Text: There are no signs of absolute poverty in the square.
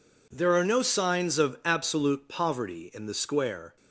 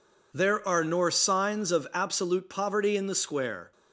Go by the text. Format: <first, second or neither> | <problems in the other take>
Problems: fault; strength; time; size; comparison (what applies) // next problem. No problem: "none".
first | says "nor" for "no"; at 0.8 s